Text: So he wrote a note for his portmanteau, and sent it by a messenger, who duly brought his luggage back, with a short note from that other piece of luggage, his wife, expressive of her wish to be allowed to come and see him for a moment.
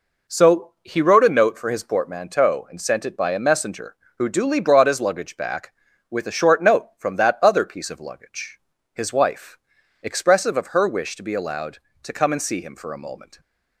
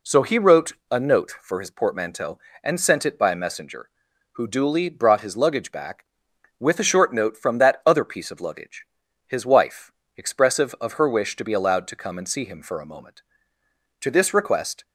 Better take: first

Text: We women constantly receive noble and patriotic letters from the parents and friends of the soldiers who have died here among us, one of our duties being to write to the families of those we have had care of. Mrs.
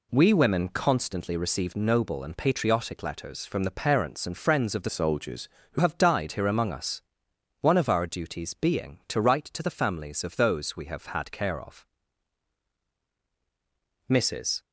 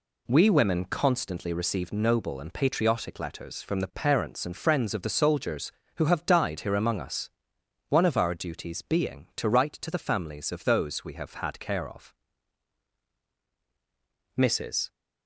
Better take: second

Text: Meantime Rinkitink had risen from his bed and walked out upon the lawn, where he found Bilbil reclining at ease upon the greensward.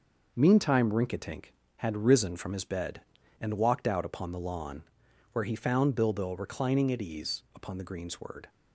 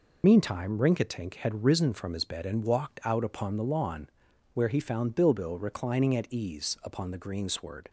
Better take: first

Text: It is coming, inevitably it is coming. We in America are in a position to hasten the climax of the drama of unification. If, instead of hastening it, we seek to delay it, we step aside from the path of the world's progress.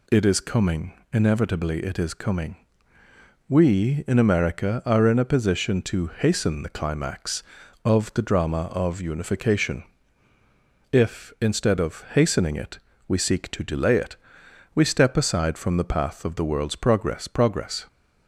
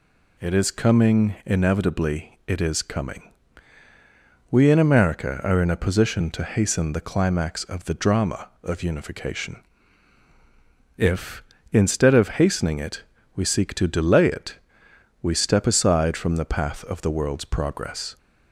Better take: second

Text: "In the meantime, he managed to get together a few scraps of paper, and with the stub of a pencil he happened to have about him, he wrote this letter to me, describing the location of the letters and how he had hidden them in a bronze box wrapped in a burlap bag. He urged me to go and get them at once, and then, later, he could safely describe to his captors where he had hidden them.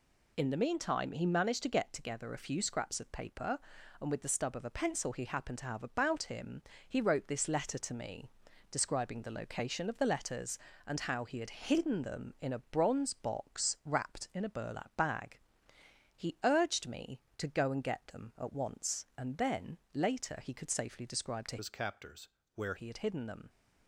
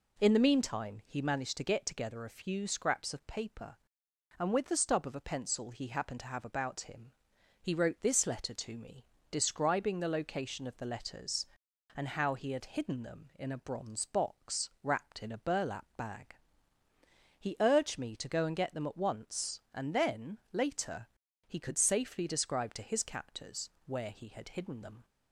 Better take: second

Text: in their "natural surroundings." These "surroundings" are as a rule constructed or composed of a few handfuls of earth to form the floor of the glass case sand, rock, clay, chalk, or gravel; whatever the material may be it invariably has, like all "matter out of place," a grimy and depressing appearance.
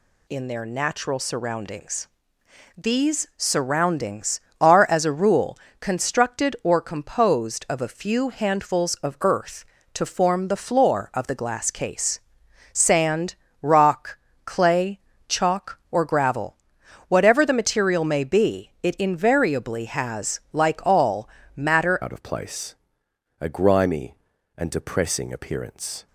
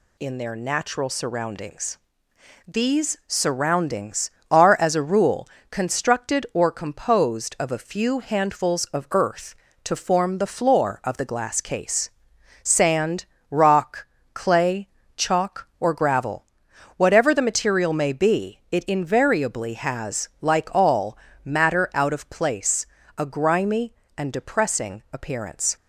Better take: second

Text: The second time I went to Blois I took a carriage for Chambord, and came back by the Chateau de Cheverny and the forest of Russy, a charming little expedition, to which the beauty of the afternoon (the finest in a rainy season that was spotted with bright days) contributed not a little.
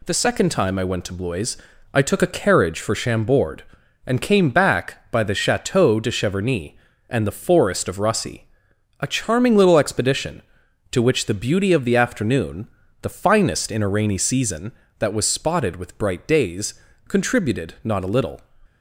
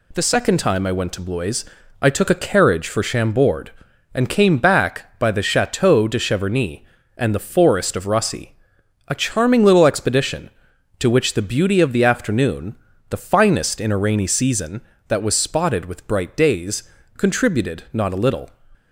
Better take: neither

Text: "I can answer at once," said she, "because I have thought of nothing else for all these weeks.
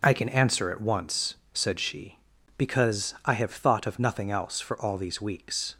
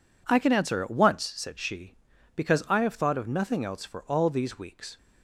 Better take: neither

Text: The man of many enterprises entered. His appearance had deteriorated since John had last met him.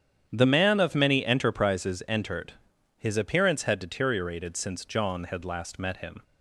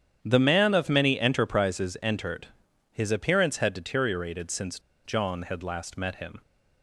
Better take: first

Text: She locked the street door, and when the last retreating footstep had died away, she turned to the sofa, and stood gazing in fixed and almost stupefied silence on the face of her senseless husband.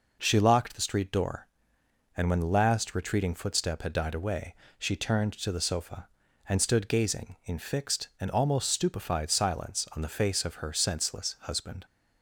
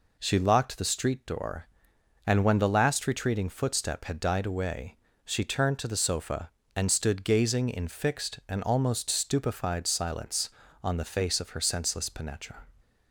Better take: first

